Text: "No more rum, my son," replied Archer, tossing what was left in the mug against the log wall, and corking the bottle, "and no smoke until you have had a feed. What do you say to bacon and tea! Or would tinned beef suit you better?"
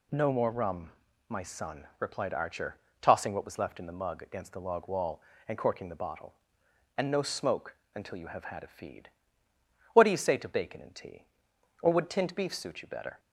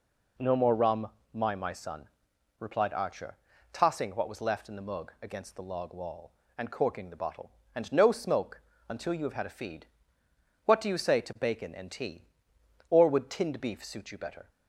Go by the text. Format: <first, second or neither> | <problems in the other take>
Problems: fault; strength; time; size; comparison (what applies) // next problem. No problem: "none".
first | says "my" twice; at 1.5 s // pauses between "smoke" and "until"; slight; at 8.6 s; 0.26 s long; slight in the first